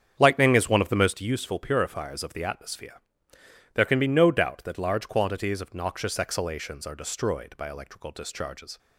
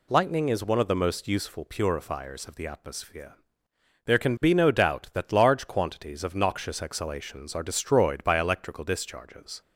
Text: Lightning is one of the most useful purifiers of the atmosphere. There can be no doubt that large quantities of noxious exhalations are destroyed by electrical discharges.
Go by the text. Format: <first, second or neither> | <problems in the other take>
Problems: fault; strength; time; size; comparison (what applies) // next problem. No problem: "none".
second | starts louder than the rest; strong; until 1.1 s; 8 dB